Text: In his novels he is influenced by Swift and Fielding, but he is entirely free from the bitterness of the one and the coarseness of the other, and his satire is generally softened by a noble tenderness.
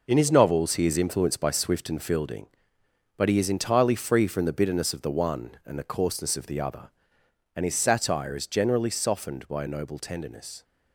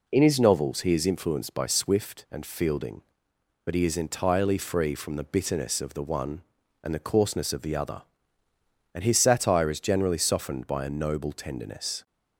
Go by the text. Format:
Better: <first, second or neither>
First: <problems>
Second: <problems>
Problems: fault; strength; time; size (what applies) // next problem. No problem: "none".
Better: second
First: gets quieter; strong; throughout; 8.5 dB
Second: none